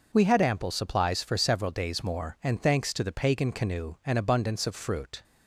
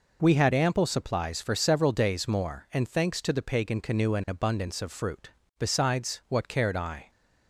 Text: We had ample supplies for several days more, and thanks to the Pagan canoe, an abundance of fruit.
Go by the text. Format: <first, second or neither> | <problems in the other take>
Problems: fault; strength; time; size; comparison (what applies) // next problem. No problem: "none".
first | goes on to say "Besides what cared I"; from 5.6 s on; 1.5 s long